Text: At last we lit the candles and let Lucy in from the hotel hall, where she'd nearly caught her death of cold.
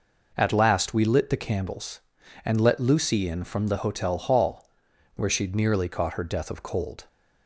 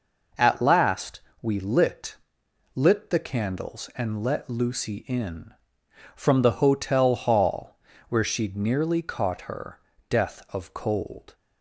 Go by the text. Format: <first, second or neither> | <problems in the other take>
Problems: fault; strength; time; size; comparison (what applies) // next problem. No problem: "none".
first | pauses between "last" and "we"; slight; at 1.2 s; 0.22 s long // says "lit" twice; at 2.7 s // pauses between "her" and "death"; slight; at 9.7 s; 0.30 s long